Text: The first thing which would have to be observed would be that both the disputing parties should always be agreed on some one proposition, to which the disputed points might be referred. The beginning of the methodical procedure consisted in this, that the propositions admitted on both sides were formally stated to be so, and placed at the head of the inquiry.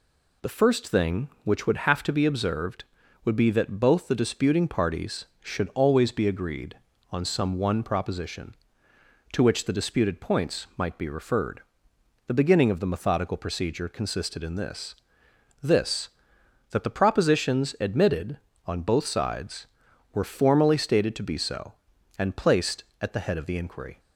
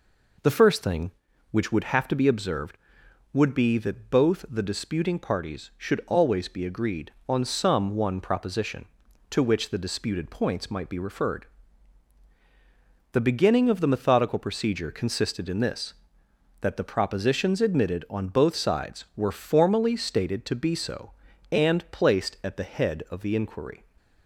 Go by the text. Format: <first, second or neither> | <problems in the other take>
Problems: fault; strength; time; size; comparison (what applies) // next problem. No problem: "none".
second | says "this" twice; at 15.6 s